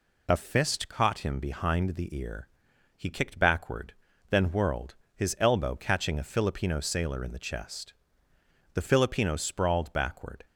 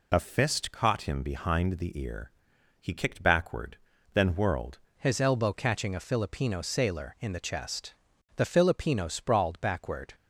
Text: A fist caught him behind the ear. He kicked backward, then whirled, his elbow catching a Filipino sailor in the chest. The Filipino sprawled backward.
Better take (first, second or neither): first